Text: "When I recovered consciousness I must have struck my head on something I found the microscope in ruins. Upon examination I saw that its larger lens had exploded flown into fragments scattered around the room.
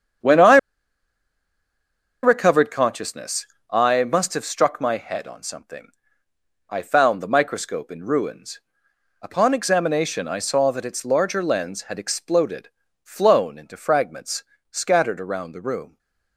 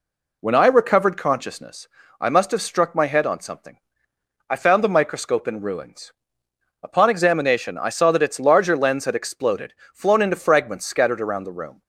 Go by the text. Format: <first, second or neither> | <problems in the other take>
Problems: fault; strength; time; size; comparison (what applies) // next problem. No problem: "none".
second | starts louder than the rest; strong; until 2.8 s; 8 dB // pauses between "I" and "recovered"; strong; at 0.5 s; 1.6 s long // pauses between "consciousness" and "I"; slight; at 3.4 s; 0.22 s long; slight in the second // pauses between "something" and "I"; noticeable; at 5.9 s; 0.80 s long; noticeable in the second // pauses between "exploded" and "flown"; slight; at 12.7 s; 0.32 s long; slight in the second // pauses between "fragments" and "scattered"; slight; at 14.4 s; 0.26 s long